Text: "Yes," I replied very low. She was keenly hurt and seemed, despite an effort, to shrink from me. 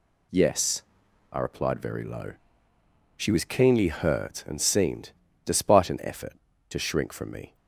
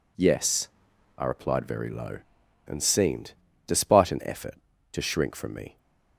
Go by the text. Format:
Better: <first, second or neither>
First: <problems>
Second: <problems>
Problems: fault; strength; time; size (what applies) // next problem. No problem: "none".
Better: first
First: none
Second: skips "She was keenly hurt"; at 2.4 s